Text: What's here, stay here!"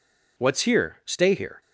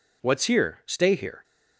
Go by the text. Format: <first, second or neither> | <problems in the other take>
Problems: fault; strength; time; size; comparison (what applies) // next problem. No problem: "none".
neither | none